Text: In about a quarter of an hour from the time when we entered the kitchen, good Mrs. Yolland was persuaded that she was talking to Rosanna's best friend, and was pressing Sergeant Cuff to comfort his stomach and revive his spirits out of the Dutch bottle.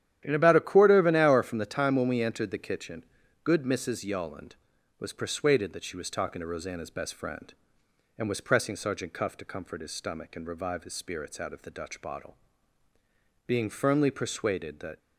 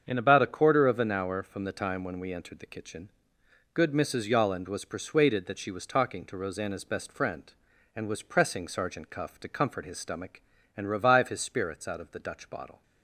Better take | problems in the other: second | starts louder than the rest; strong; until 1.2 s; 11 dB; strong in the second // goes on to say "Being firmly persuaded that"; from 13.4 s on; 1.5 s long

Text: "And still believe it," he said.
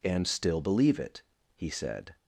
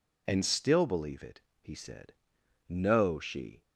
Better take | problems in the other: first | goes on to say "No she"; noticeable; from 2.6 s on; 0.94 s long

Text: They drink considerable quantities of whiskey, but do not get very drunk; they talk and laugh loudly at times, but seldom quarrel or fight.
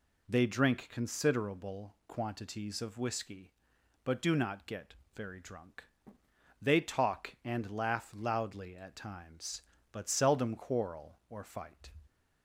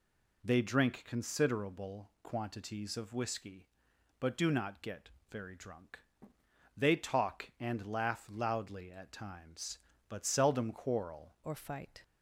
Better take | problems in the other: first | pauses between "get" and "very"; slight; at 5.0 s; 0.20 s long; slight in the first // changes voice at "or"; from 11.4 s on; 0.6 s long

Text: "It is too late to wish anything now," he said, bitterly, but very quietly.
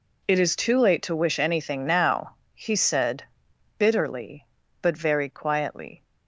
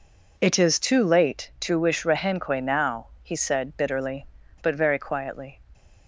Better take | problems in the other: first | says "rehenque" for "anything"; at 2.0 s

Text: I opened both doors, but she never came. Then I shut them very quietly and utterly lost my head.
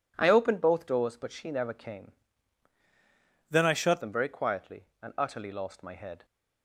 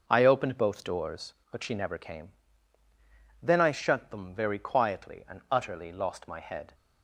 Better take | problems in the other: second | changes voice from "Then" to "shut"; from 3.4 to 4.0 s; 0.6 s long

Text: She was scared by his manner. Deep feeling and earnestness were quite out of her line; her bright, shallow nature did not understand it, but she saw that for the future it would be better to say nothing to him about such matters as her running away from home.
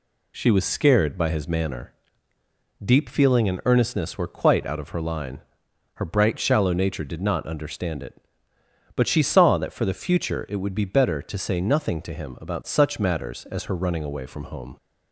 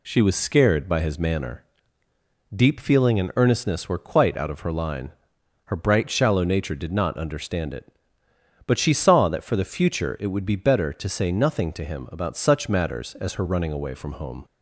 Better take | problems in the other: neither | none

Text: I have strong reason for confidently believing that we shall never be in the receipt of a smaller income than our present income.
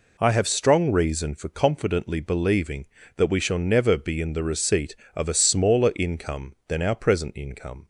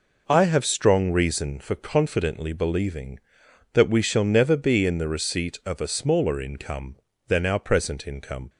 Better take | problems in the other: neither | none

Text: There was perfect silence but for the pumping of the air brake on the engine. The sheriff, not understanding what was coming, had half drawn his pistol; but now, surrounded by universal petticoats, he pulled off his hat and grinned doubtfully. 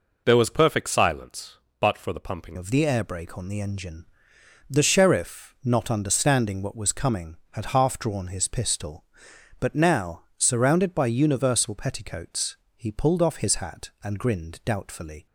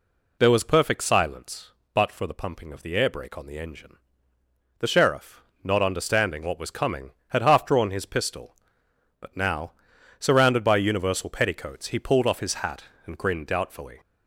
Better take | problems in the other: second | changes voice at "of"; from 2.5 s on; 12.7 s long

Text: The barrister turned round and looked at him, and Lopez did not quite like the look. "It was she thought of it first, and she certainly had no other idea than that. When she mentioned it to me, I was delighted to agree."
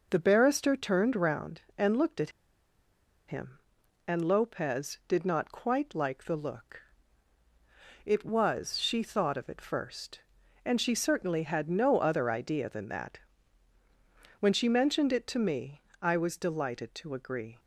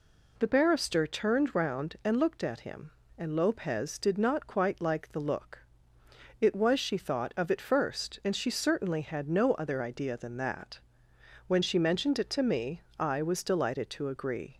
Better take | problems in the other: second | pauses between "at" and "him"; noticeable; at 2.3 s; 0.97 s long

